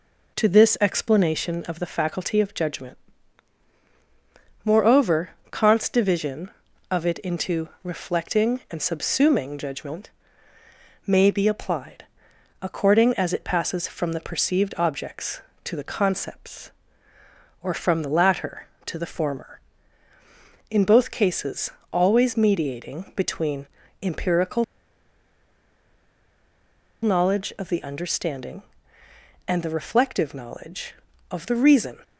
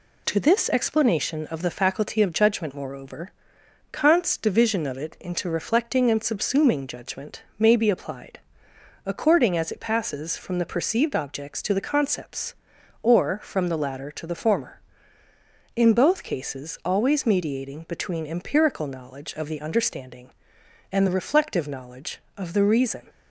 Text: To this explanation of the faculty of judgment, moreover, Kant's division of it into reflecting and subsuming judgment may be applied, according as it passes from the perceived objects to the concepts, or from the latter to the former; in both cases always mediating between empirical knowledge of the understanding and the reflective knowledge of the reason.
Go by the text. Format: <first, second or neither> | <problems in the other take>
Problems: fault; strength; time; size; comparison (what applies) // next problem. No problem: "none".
second | pauses between "into" and "reflecting"; slight; at 7.6 s; 0.16 s long // pauses between "judgment" and "may"; noticeable; at 10.0 s; 0.96 s long; slight in the second // pauses between "cases" and "always"; slight; at 21.6 s; 0.22 s long // pauses between "between" and "empirical"; slight; at 23.6 s; 0.34 s long // pauses between "empirical" and "knowledge"; strong; at 24.6 s; 2.3 s long